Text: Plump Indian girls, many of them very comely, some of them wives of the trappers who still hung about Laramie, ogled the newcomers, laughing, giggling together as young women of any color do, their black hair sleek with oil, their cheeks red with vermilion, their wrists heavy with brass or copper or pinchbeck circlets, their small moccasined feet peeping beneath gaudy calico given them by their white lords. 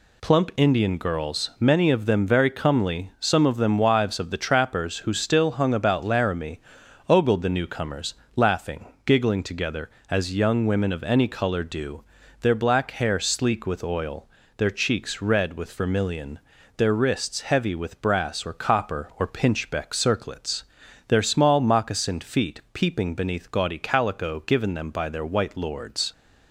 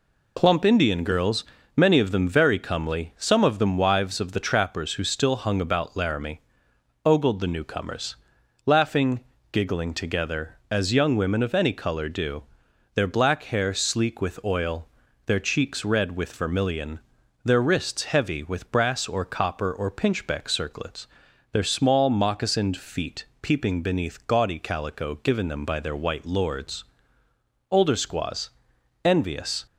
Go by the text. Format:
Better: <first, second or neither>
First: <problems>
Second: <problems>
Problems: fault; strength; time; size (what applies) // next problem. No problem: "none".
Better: first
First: none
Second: pauses between "feet" and "peeping"; slight; at 23.2 s; 0.16 s long // goes on to say "Older squaws envious"; strong; from 27.7 s on; 1.9 s long